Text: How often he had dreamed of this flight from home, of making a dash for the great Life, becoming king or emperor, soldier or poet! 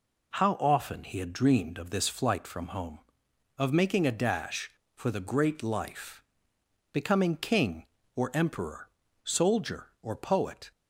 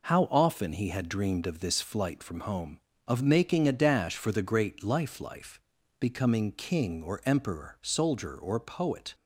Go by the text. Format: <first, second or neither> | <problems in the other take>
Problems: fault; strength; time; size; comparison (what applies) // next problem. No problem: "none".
first | says "Life" twice; at 5.2 s